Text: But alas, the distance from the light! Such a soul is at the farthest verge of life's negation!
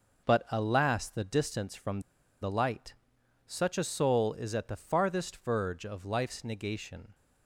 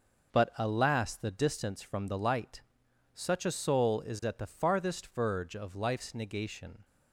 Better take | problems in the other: second | pauses between "from" and "the"; at 1.9 s; 0.42 s long

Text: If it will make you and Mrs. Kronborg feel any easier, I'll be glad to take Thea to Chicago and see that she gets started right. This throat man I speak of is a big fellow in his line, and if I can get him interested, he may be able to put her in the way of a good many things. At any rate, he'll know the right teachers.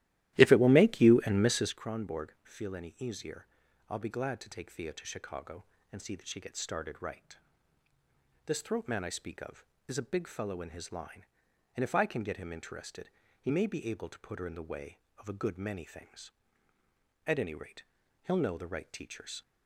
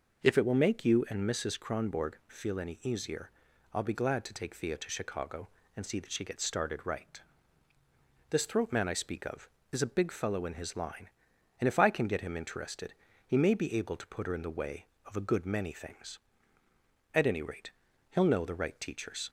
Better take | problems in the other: second | starts louder than the rest; strong; until 1.8 s; 15 dB

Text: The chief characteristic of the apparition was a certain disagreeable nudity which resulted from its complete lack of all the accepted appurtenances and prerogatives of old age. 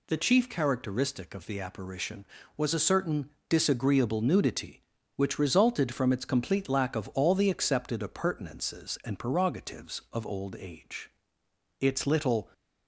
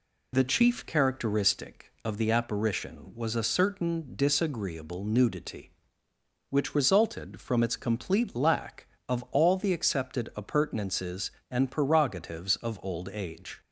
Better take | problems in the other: second | pauses between "certain" and "disagreeable"; slight; at 3.2 s; 0.20 s long // goes on to say "Its little"; noticeable; from 11.8 s on; 0.68 s long

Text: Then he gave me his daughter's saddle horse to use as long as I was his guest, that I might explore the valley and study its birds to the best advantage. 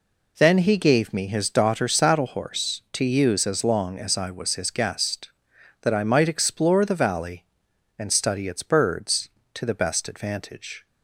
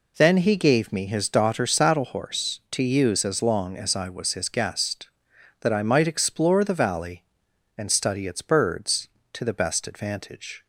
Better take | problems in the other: neither | none

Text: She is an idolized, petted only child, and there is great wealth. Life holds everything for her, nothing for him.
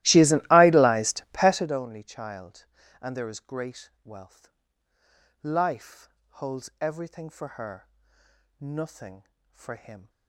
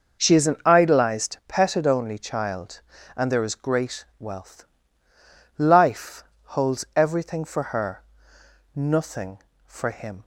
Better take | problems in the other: second | starts louder than the rest; strong; until 1.8 s; 16.5 dB // pauses between "Life" and "holds"; slight; at 6.0 s; 0.18 s long; slight in the second

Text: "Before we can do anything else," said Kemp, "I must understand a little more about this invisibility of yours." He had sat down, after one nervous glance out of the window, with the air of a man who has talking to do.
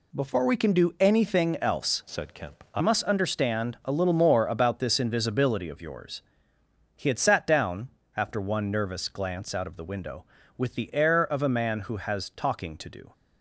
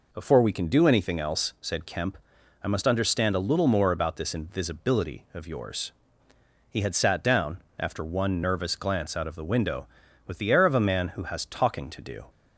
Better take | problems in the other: second | changes voice from "said" to "I"; from 2.0 to 2.8 s; 0.8 s long

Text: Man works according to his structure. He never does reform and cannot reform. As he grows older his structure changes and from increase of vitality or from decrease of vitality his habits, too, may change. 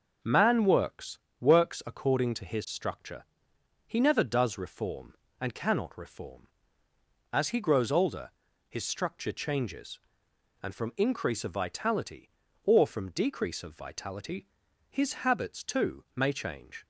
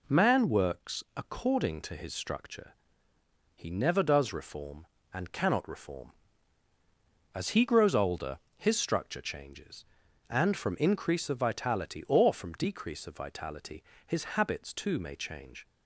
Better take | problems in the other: second | starts louder than the rest; until 1.4 s; 6 dB // says "works" twice; at 1.3 s // pauses between "older" and "his"; at 8.2 s; 0.40 s long; slight in the second // pauses between "vitality" and "his"; noticeable; at 14.4 s; 0.46 s long; slight in the second

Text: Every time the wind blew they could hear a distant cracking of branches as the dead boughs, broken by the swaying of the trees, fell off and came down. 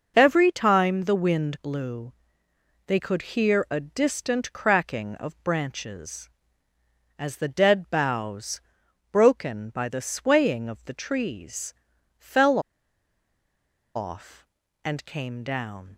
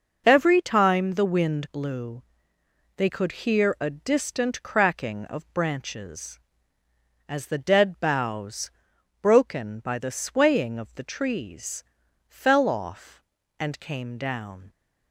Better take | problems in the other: second | pauses between "blew" and "they"; noticeable; at 2.1 s; 0.74 s long; noticeable in the second // pauses between "fell" and "off"; strong; at 12.5 s; 1.3 s long

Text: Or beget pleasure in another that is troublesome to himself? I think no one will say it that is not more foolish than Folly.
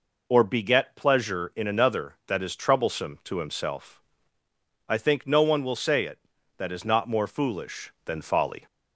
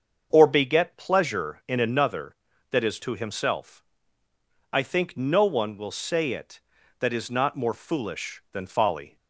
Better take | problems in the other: first | starts louder than the rest; until 1.3 s; 6.5 dB // skips "troublesome"; at 2.9 s

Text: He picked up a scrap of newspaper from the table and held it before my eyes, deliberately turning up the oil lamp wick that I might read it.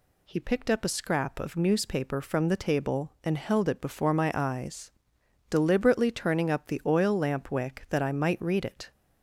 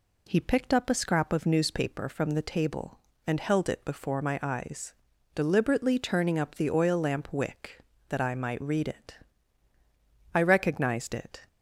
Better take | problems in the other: first | goes on to say "I recognized it"; noticeable; from 10.3 s on; 1.1 s long

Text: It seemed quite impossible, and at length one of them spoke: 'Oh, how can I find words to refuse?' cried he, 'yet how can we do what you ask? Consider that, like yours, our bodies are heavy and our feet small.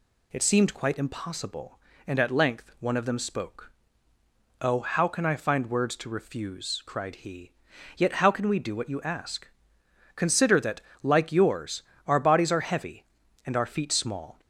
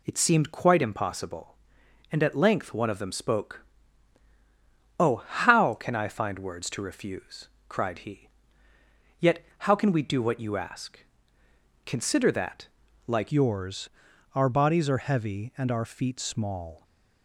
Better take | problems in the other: first | changes voice at "yours"; from 13.3 s on; 3.5 s long

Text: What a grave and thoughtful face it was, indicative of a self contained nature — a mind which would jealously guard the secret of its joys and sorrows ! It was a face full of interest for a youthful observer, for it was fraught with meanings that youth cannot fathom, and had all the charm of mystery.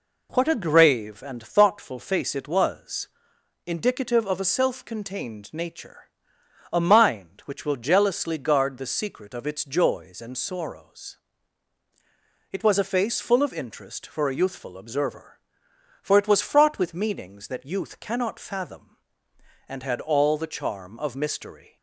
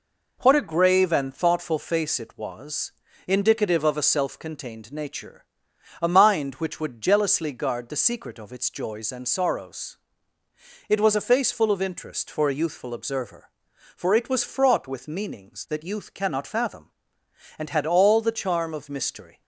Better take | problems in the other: second | says "will" for "would"; at 7.6 s

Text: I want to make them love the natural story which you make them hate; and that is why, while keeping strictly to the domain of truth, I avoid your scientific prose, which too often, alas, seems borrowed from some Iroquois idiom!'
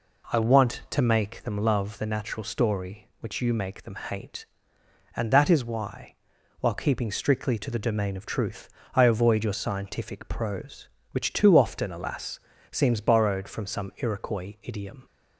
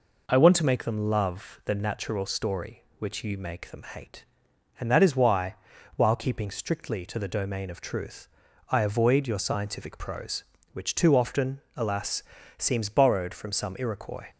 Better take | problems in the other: first | stops before "idiom"; at 14.2 s

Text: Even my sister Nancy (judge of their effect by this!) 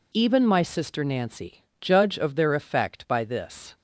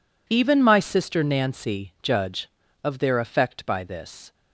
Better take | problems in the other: neither | none

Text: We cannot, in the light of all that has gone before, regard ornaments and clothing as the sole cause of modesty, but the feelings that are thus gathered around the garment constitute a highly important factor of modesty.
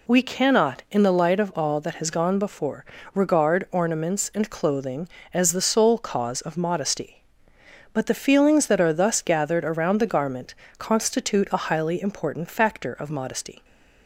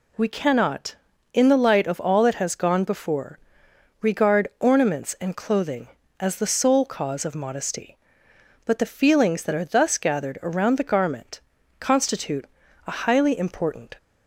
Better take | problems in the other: first | pauses between "garment" and "constitute"; noticeable; at 11.3 s; 0.66 s long; slight in the first // pauses between "constitute" and "a"; at 12.4 s; 0.40 s long // stops before "factor of modesty"; at 13.9 s

